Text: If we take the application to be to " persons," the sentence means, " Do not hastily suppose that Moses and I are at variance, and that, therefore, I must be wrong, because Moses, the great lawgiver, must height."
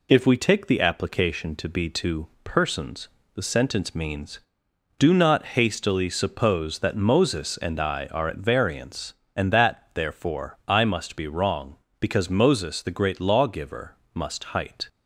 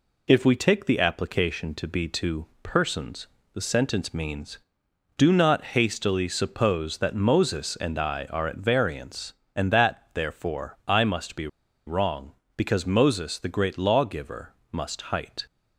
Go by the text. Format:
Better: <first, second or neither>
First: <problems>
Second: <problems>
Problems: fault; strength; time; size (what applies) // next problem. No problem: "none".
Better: first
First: none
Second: pauses between "be" and "wrong"; at 11.4 s; 0.39 s long